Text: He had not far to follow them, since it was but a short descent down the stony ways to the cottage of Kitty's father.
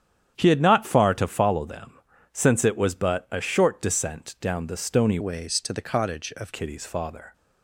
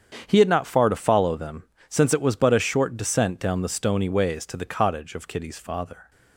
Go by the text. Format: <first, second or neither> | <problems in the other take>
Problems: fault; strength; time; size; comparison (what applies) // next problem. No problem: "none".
second | starts louder than the rest; strong; until 1.3 s; 9 dB; strong in the second // changes voice from "ways" to "of"; from 5.2 to 6.5 s; 1.3 s long